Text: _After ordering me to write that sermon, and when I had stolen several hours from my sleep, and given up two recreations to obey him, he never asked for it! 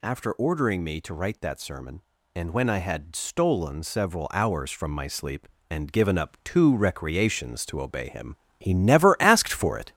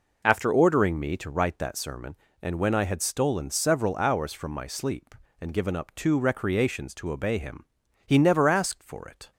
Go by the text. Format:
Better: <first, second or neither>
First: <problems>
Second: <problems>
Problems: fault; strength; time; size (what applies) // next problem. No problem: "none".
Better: second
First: gets louder; noticeable; throughout; 4 dB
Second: none